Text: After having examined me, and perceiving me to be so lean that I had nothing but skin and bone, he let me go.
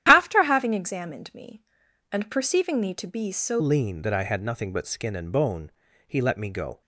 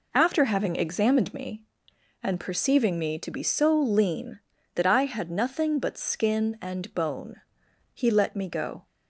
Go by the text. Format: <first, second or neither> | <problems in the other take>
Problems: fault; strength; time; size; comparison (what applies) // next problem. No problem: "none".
second | starts louder than the rest; strong; until 1.1 s; 11 dB // changes voice at "lean"; from 3.5 s on; 3.3 s long